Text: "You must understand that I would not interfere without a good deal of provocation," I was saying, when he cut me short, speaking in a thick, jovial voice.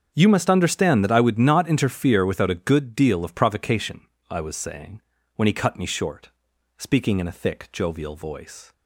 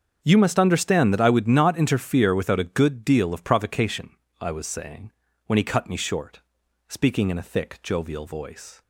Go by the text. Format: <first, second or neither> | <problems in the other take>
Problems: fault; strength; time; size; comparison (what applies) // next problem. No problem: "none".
neither | starts louder than the rest; the same in both